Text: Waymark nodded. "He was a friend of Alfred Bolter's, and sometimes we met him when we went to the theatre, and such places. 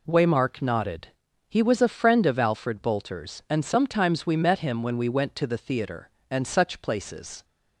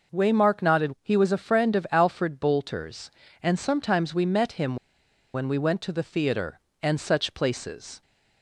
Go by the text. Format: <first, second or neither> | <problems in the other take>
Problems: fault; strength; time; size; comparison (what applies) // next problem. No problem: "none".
first | pauses between "him" and "when"; noticeable; at 4.7 s; 0.59 s long